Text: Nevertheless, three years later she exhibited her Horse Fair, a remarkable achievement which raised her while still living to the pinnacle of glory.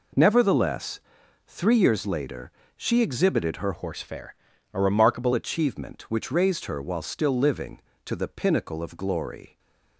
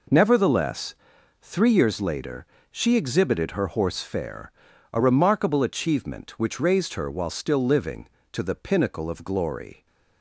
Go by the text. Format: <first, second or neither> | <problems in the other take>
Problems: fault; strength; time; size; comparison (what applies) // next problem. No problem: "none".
second | pauses between "later" and "she"; slight; at 2.5 s; 0.24 s long; slight in the second // changes voice from "Horse" to "remarkable"; from 3.7 to 5.3 s; 1.6 s long // stays silent after the last word; slight; from 9.4 s on; 0.5 s long